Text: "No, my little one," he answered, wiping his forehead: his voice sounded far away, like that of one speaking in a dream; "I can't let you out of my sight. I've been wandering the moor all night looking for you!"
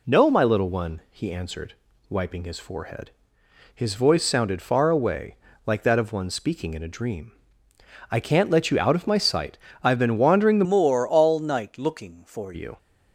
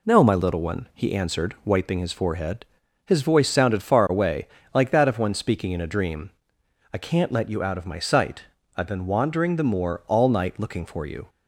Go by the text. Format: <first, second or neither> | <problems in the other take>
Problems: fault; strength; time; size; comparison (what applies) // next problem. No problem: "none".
second | changes voice from "moor" to "for"; from 10.6 to 12.5 s; 1.9 s long